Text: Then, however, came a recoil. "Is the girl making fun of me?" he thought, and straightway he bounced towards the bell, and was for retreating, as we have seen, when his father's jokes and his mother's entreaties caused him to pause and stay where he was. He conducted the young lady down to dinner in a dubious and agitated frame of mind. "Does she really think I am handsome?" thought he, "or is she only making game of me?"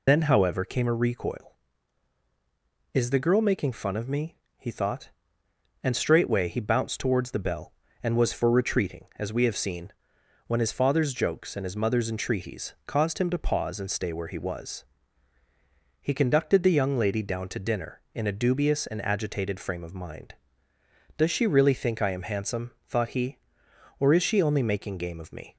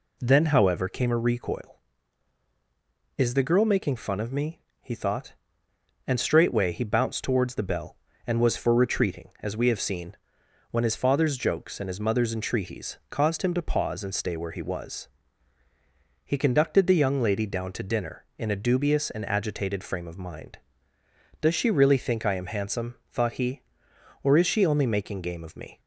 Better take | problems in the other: second | loses the start of "Then"; at 0.0 s; 120 ms

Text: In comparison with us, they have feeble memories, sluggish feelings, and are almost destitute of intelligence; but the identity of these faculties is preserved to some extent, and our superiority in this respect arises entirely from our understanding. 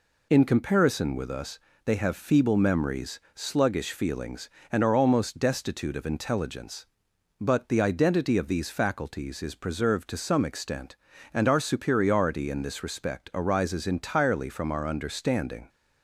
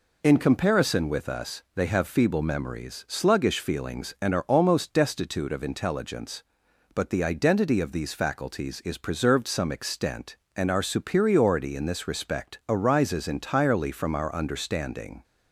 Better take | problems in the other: first | skips "to"; at 9.4 s

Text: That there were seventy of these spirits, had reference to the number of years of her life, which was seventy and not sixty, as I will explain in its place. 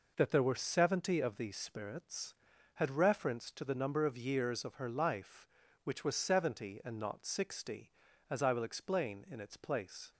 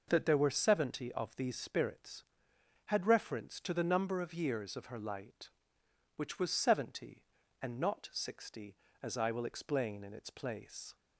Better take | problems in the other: first | says "light" for "life"; at 4.9 s

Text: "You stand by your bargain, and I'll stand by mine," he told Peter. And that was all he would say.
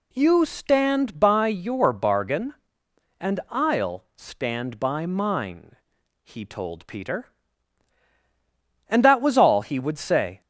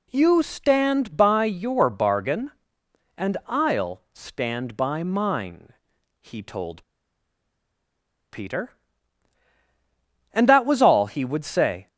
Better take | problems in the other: first | pauses between "told" and "Peter"; strong; at 6.8 s; 1.4 s long

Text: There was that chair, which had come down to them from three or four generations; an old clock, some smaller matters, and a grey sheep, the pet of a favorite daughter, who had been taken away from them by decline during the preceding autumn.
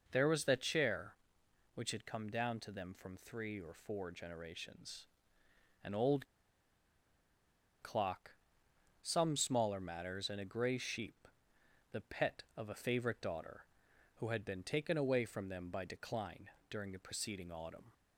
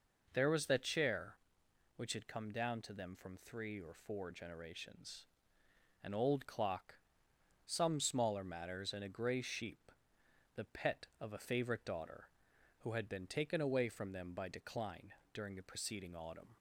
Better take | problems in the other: second | pauses between "old" and "clock"; strong; at 6.2 s; 1.5 s long // pauses between "decline" and "during"; slight; at 16.4 s; 0.20 s long; slight in the second

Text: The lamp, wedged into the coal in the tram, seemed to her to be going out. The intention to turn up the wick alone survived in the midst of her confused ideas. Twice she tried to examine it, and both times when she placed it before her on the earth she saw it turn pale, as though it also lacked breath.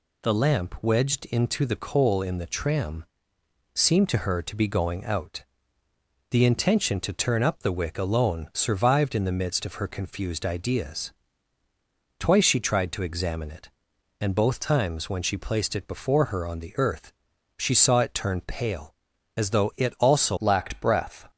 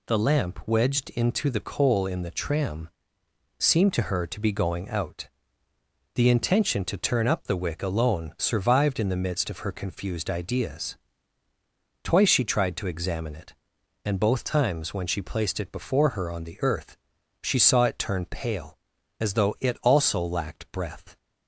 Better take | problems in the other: second | pauses between "earth" and "she"; noticeable; at 17.1 s; 0.46 s long; noticeable in the second // changes voice at "lacked"; from 20.3 s on; 0.9 s long

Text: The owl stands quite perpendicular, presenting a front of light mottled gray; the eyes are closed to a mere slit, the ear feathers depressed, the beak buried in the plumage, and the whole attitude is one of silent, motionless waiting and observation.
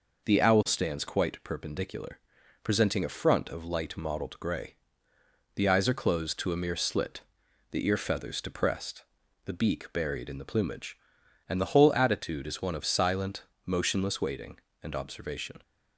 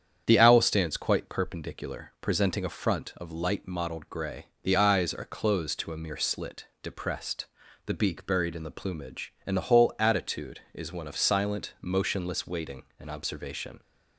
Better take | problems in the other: first | starts louder than the rest; strong; until 1.2 s; 8.5 dB // skips "the ear feathers"; at 6.7 s

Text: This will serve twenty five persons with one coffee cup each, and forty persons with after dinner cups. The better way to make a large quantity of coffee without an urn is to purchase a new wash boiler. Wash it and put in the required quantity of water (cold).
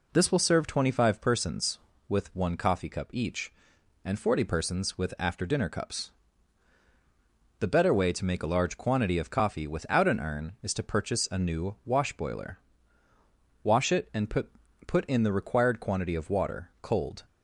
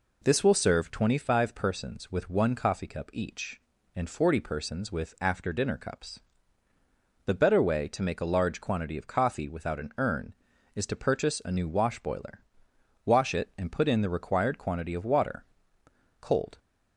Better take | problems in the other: second | says "put" twice; at 14.8 s

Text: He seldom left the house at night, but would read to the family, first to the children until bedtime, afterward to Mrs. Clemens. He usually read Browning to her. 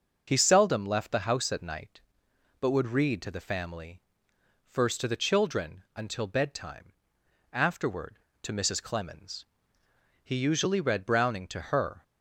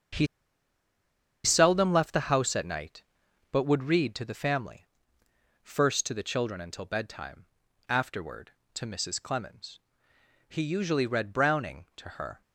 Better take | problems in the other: first | starts louder than the rest; until 2.3 s; 7 dB // pauses between "He" and "seldom"; at 0.2 s; 1.1 s long

